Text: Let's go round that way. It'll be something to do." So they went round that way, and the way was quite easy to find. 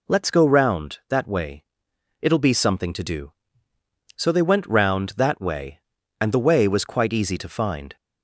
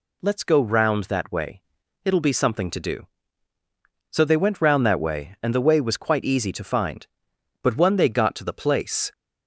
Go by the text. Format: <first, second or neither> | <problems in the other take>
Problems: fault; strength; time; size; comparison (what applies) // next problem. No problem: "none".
first | goes on to say "But when they got to the place"; from 7.6 s on; 1.5 s long